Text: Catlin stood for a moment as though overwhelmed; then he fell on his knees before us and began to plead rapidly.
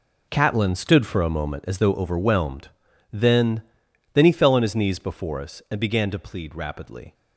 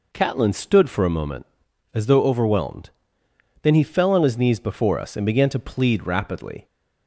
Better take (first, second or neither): second